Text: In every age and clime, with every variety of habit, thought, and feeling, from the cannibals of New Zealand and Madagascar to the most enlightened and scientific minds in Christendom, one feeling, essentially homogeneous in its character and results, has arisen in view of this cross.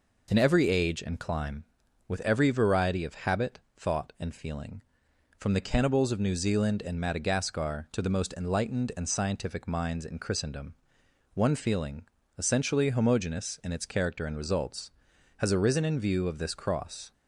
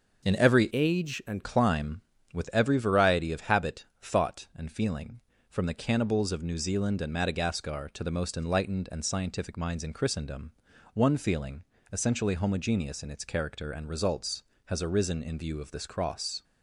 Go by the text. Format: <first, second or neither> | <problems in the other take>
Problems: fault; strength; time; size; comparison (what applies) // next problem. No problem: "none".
first | starts louder than the rest; until 1.3 s; 6 dB // changes voice from "age" to "and"; from 0.7 to 1.4 s; 0.7 s long